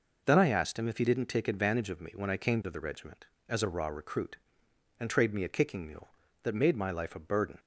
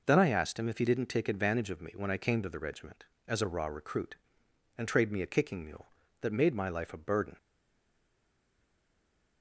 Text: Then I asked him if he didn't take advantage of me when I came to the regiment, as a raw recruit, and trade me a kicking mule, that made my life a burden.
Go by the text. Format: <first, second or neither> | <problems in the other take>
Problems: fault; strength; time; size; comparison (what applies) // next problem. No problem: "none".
first | stays silent after the last word; noticeable; from 7.3 s on; 2.1 s long